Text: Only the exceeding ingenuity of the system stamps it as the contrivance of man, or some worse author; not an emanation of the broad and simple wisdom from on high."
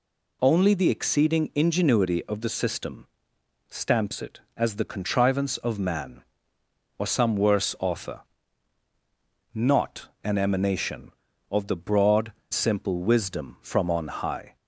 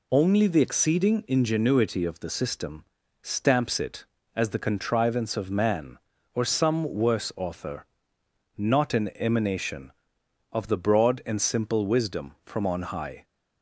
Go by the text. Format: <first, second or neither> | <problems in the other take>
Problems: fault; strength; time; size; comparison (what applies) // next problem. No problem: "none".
second | pauses between "system" and "stamps"; noticeable; at 3.0 s; 0.62 s long; also in the second // pauses between "not" and "an"; slight; at 10.0 s; 0.16 s long // skips "and"; at 12.4 s